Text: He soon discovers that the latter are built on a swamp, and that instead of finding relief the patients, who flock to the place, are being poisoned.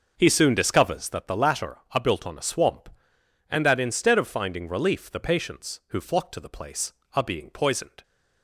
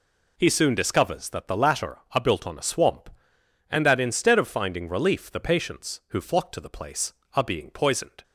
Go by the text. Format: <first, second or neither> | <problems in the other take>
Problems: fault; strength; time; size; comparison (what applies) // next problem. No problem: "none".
second | starts louder than the rest; noticeable; until 1.3 s; 6 dB